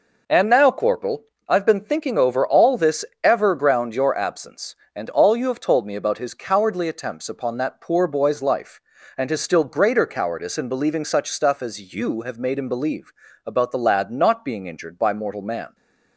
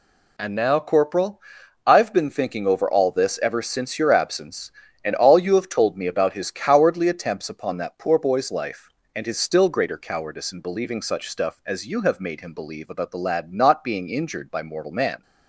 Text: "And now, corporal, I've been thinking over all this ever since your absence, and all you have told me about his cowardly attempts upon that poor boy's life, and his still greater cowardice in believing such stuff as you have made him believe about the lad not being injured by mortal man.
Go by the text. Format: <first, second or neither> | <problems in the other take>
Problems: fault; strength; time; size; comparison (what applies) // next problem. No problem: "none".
second | pauses between "this" and "ever"; slight; at 3.0 s; 0.18 s long // says "ground" for "since"; at 3.5 s // pauses between "believe" and "about"; slight; at 13.1 s; 0.32 s long